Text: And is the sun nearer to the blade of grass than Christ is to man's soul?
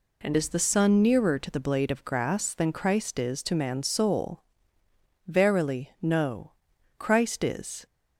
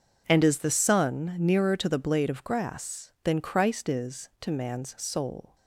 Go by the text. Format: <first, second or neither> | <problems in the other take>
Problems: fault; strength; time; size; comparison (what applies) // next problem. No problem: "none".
second | goes on to say "Verily no Christ is"; strong; from 5.2 s on; 2.5 s long